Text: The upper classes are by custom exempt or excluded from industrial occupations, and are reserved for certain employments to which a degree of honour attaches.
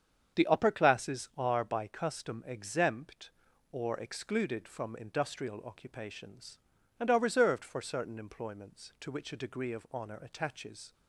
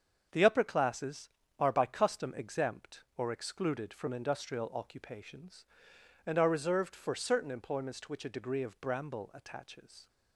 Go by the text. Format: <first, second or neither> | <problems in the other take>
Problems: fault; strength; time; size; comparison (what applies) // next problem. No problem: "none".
first | starts louder than the rest; until 1.5 s; 7 dB; strong in the first // says "bramble" for "honour"; at 8.7 s